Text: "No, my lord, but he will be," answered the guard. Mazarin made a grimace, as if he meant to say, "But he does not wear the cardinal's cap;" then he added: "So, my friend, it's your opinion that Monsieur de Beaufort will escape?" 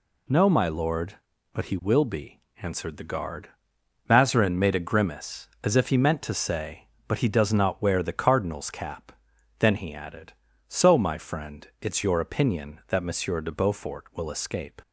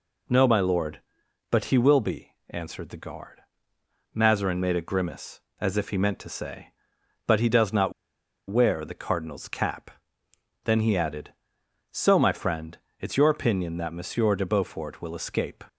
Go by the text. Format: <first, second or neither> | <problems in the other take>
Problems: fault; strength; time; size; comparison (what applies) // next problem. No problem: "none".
first | pauses between "not" and "wear"; noticeable; at 7.9 s; 0.57 s long